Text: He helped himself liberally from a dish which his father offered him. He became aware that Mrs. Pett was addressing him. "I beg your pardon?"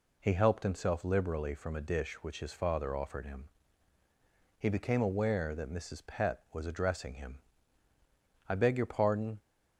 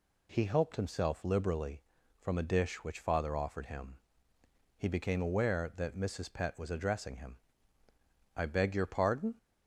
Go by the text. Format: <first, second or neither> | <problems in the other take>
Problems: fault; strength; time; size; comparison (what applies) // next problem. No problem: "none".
first | skips "his"; at 3.0 s